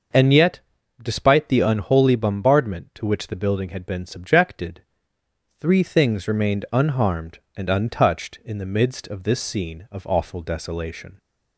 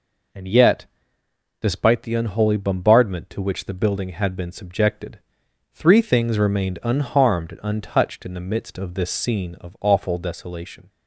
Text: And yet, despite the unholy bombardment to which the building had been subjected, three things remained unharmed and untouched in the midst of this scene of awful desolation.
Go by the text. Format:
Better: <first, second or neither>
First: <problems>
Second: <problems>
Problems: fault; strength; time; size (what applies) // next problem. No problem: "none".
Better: neither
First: none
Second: none